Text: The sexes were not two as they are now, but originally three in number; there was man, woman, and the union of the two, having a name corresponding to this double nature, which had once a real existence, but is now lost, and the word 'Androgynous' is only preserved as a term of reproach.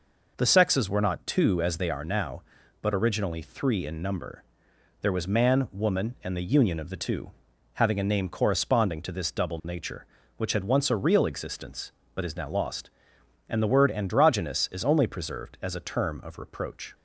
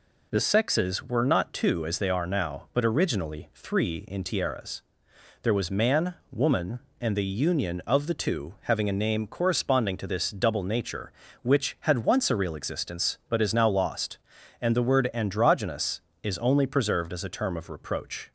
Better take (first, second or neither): first